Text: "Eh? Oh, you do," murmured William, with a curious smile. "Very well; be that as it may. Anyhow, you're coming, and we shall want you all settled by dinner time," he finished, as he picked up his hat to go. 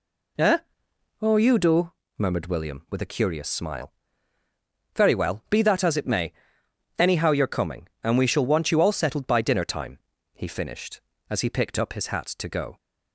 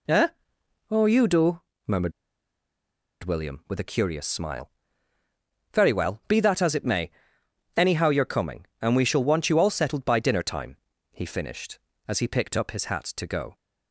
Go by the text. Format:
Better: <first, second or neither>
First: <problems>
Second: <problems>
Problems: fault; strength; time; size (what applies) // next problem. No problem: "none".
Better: first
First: none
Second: pauses between "murmured" and "William"; at 2.1 s; 1.1 s long